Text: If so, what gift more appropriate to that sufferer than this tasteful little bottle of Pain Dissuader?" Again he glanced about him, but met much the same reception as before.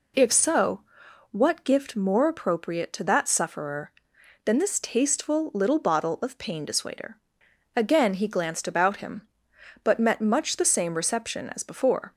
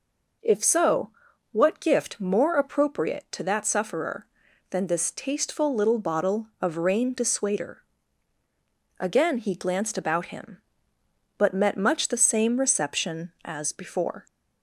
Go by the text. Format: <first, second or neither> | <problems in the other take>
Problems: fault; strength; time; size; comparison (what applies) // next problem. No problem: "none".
first | says "Rain" for "Pain"; at 6.7 s